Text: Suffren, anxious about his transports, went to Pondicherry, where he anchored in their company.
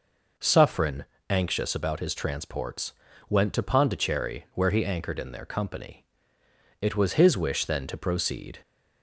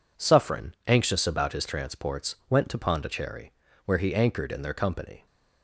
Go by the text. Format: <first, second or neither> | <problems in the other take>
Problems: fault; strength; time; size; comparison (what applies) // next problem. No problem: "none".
second | goes on to say "It was his wish then to proceed"; strong; from 6.8 s on; 1.7 s long